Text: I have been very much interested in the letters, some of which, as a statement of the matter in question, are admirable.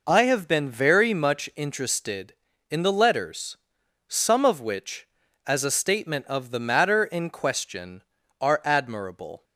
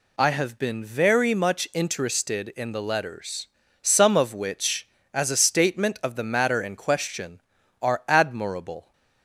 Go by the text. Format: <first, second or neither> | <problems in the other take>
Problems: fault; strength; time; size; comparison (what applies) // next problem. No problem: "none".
neither | none